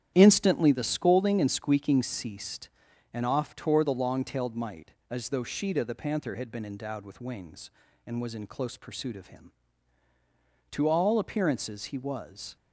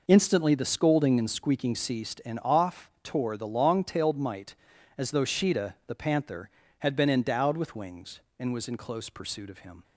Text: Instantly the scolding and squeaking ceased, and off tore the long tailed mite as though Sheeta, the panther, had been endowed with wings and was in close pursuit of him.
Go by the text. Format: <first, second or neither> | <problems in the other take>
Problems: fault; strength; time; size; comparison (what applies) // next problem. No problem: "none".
second | starts louder than the rest; strong; until 1.1 s; 10 dB // goes on to say "To all appearances he was"; strong; from 10.7 s on; 1.8 s long